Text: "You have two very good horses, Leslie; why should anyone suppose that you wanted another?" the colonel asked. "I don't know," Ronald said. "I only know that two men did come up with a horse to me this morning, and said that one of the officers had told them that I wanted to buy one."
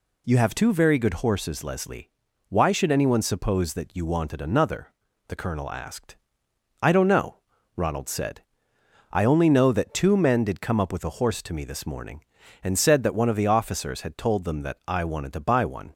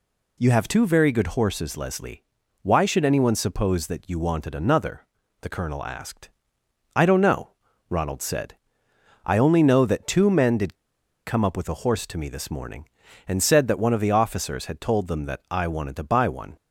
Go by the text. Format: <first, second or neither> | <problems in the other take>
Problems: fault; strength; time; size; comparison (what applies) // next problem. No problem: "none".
first | pauses between "did" and "come"; noticeable; at 10.7 s; 0.53 s long